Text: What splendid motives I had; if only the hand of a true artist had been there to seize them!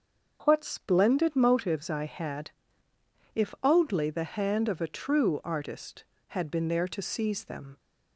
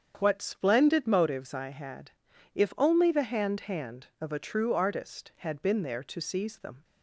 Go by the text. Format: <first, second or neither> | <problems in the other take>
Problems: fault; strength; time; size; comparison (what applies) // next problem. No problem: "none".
first | starts louder than the rest; strong; until 1.1 s; 7.5 dB; also in the first // says "hand" twice; at 3.6 s